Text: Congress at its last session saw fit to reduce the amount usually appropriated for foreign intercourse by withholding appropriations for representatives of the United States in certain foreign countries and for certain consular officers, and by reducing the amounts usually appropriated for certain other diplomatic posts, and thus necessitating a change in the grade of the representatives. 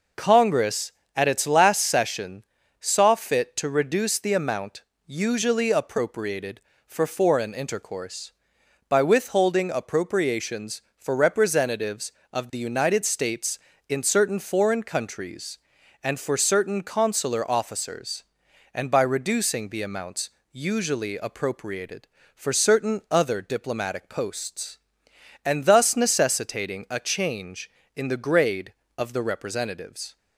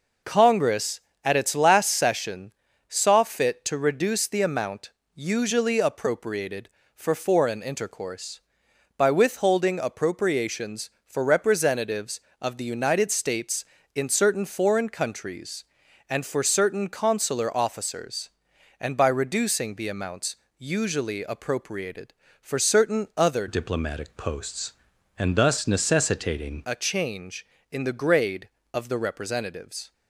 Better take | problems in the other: first | pauses between "session" and "saw"; slight; at 2.5 s; 0.36 s long; slight in the first // pauses between "amount" and "usually"; slight; at 4.9 s; 0.24 s long; slight in the first // pauses between "amounts" and "usually"; slight; at 20.3 s; 0.22 s long; slight in the first // changes voice from "diplomatic" to "necessitating"; from 23.4 to 26.6 s; 3.2 s long

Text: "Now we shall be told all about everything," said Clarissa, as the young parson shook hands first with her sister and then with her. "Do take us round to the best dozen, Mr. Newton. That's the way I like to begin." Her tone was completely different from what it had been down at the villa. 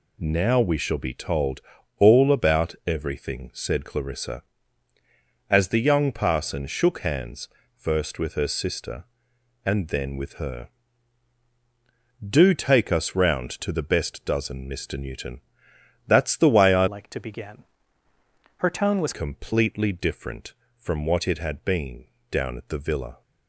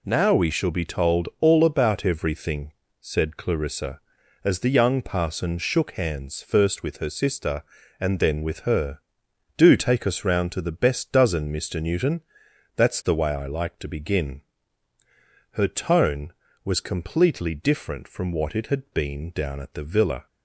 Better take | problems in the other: second | pauses between "told" and "all"; slight; at 1.6 s; 0.36 s long // pauses between "hands" and "first"; slight; at 7.4 s; 0.28 s long // changes voice from "like" to "was"; from 16.8 to 19.1 s; 2.3 s long // pauses between "been" and "down"; slight; at 22.0 s; 0.22 s long

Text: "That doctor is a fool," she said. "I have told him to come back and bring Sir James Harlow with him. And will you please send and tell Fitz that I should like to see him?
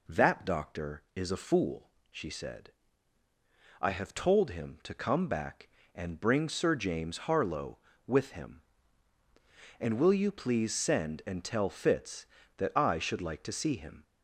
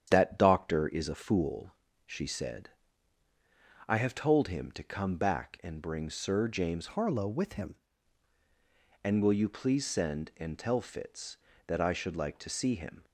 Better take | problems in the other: first | starts louder than the rest; strong; until 1.1 s; 9 dB // changes voice from "Harlow" to "him"; from 6.8 to 7.7 s; 0.9 s long

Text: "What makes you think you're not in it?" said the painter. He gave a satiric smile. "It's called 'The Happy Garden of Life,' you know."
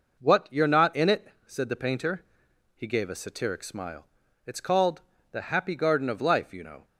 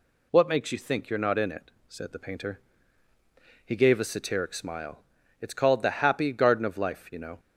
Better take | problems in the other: second | skips "makes you think"; at 0.4 s // pauses between "called" and "The"; slight; at 5.0 s; 0.30 s long

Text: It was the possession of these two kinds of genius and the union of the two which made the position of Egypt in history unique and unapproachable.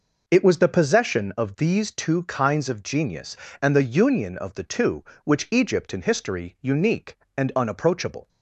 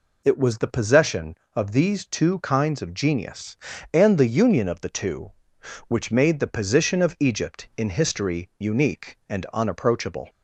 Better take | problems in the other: second | skips "made the position of"; at 5.4 s

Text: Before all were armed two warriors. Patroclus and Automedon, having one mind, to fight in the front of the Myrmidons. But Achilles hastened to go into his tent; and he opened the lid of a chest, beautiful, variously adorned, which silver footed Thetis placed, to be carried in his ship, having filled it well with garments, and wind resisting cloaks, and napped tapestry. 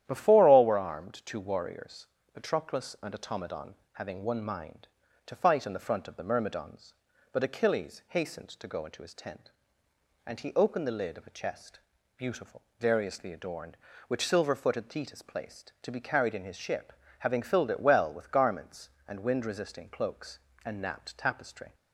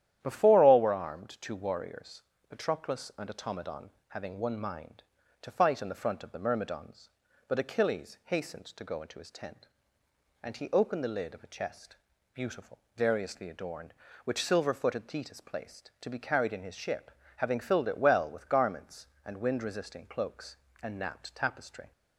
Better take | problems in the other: neither | starts louder than the rest; strong; the same in both

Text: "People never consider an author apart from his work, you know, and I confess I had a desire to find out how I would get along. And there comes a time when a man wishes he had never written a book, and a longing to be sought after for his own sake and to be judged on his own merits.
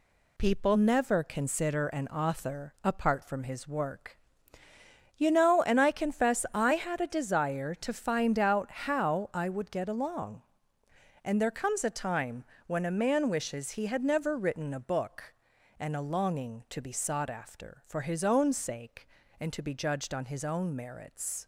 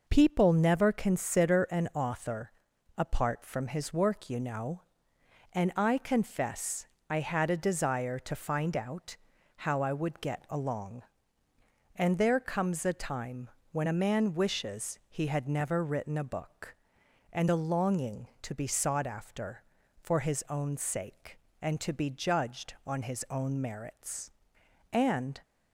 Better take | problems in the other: first | pauses between "author" and "apart"; at 2.5 s; 0.44 s long // pauses between "confess" and "I"; slight; at 6.8 s; 0.22 s long // pauses between "out" and "how"; at 9.1 s; 0.40 s long // pauses between "time" and "when"; slight; at 13.4 s; 0.24 s long; slight in the first // goes on to say "And"; slight; from 24.9 s on; 0.48 s long

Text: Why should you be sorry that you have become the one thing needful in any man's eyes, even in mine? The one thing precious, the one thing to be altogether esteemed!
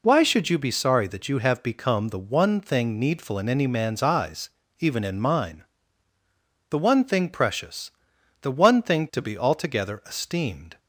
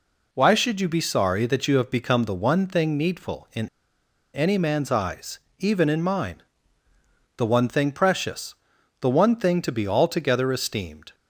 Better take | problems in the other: first | pauses between "in" and "any"; noticeable; at 3.6 s; 0.65 s long

